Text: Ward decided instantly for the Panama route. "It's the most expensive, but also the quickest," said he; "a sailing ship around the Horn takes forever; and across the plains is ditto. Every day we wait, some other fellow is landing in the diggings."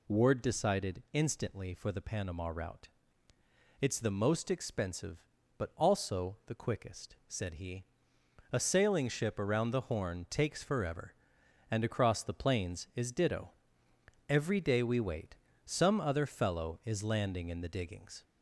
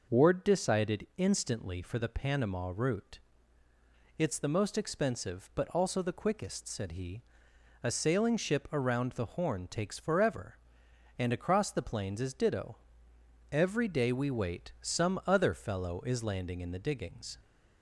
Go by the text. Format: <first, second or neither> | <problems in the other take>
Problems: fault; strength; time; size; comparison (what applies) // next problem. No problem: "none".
second | gets louder; slight; throughout; 2.5 dB